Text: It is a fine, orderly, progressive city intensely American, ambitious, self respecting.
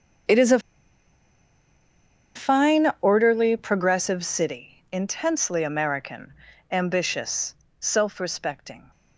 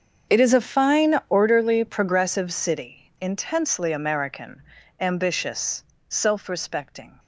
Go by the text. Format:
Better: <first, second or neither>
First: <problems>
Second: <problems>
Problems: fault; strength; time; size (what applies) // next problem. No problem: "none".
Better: second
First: starts louder than the rest; strong; until 3.1 s; 7.5 dB // pauses between "a" and "fine"; strong; at 0.5 s; 1.7 s long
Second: starts louder than the rest; strong; until 1.4 s; 7 dB